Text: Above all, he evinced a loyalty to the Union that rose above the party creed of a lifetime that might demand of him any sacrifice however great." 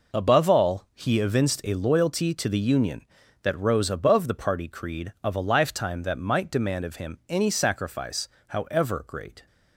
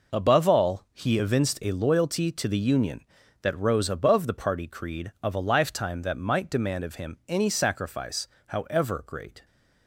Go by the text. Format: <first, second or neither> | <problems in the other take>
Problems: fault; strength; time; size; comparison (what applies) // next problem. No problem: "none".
neither | pauses between "sacrifice" and "however"; slight; the same in both